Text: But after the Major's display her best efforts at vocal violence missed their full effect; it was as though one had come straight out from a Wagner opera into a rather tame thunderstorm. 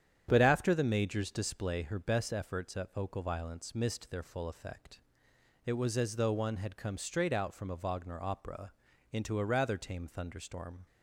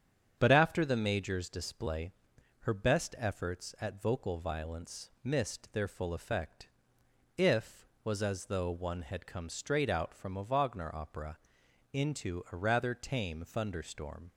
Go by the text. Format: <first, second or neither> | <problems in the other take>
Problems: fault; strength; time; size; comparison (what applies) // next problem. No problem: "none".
first | starts louder than the rest; strong; until 1.4 s; 8 dB; strong in the first // pauses between "display" and "her"; noticeable; at 2.1 s; 0.48 s long // says "if" for "it"; at 7.3 s // pauses between "opera" and "into"; noticeable; at 11.3 s; 0.54 s long; also in the first